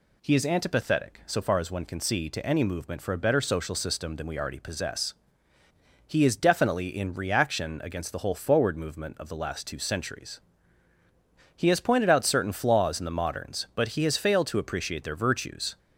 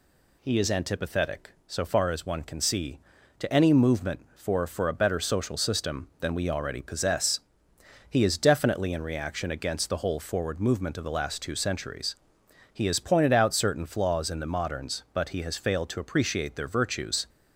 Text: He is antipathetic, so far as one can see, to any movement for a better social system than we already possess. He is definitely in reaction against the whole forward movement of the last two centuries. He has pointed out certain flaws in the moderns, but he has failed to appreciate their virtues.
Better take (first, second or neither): first